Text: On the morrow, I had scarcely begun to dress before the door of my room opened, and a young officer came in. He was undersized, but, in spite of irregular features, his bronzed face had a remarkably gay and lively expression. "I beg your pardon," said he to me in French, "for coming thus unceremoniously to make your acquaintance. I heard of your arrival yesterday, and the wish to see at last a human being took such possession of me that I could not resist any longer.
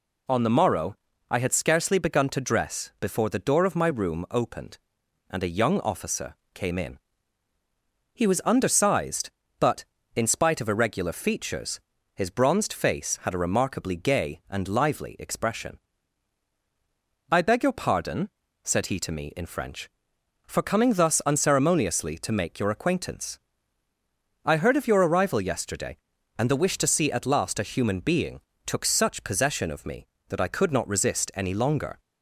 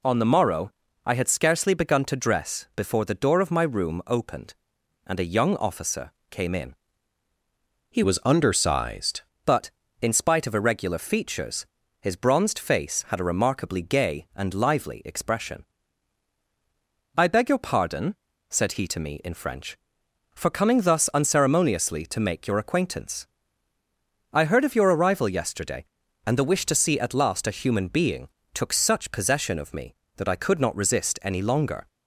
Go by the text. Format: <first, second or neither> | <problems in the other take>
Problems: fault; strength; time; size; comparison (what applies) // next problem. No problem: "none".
first | pauses between "officer" and "came"; slight; at 6.1 s; 0.18 s long; slight in the first // changes voice from "was" to "undersized"; from 8.0 to 9.2 s; 1.2 s long // pauses between "being" and "took"; slight; at 28.2 s; 0.24 s long; slight in the first